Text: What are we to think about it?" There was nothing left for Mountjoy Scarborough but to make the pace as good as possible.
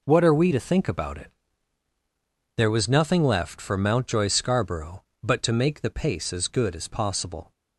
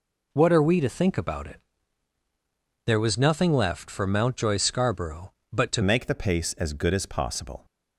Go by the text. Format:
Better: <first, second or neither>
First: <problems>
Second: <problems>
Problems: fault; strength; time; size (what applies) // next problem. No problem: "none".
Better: first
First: none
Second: changes voice at "make"; from 5.8 s on; 1.8 s long